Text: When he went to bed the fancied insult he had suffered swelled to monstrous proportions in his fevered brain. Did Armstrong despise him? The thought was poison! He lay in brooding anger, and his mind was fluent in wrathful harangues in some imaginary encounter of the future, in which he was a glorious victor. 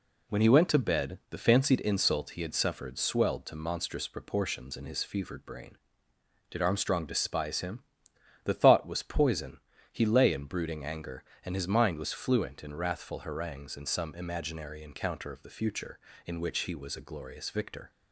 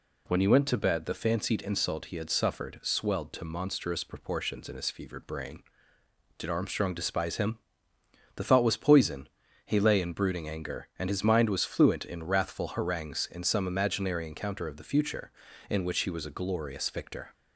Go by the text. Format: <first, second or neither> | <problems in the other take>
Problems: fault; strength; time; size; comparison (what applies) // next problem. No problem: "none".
neither | none